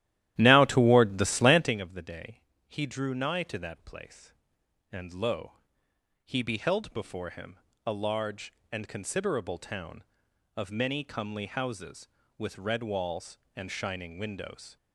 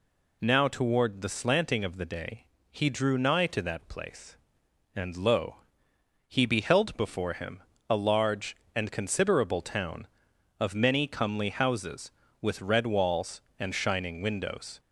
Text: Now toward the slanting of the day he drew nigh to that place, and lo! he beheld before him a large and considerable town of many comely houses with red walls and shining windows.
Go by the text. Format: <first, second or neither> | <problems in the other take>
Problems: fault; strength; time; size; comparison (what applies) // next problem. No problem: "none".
second | starts louder than the rest; strong; until 1.8 s; 13 dB // pauses between "day" and "he"; slight; at 2.4 s; 0.26 s long; slight in the second // pauses between "him" and "a"; slight; at 7.5 s; 0.28 s long; slight in the second